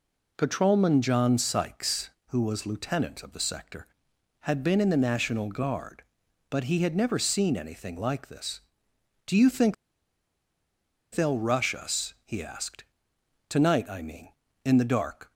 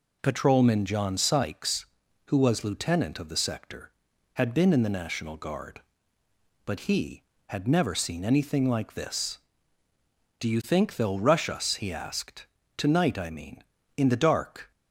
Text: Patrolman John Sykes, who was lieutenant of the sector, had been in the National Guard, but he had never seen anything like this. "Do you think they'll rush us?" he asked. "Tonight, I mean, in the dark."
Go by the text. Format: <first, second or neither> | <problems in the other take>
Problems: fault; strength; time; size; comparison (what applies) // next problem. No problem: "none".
second | pauses between "think" and "they'll"; strong; at 9.7 s; 1.3 s long